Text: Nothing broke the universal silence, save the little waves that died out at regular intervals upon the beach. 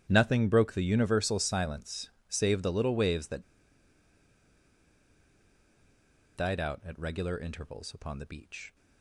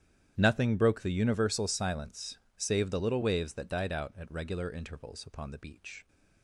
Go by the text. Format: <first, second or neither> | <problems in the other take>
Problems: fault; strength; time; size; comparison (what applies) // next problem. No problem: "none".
second | starts louder than the rest; strong; until 1.1 s; 10 dB; strong in the second // pauses between "that" and "died"; strong; at 3.4 s; 2.9 s long